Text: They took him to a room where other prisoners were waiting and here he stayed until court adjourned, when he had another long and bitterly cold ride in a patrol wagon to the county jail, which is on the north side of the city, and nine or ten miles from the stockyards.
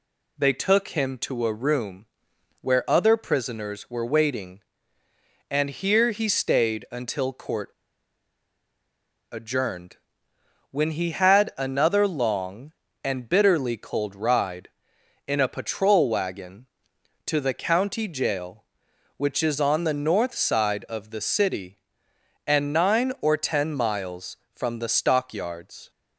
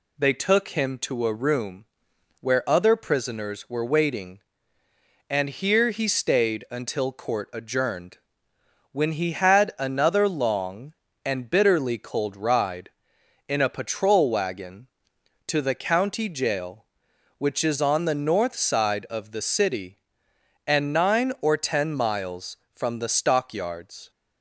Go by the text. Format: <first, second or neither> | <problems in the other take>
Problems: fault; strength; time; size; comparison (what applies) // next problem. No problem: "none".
second | pauses between "room" and "where"; noticeable; at 2.0 s; 0.54 s long; noticeable in the second // pauses between "court" and "adjourned"; strong; at 7.6 s; 1.6 s long